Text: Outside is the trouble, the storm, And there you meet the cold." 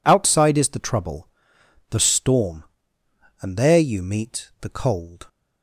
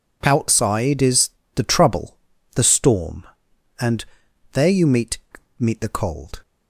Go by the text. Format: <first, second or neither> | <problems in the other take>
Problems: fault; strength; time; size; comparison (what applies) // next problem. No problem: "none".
first | pauses between "is" and "the"; slight; at 1.2 s; 0.26 s long // pauses between "And" and "there"; noticeable; at 4.0 s; 0.46 s long // says "meet" twice; at 5.5 s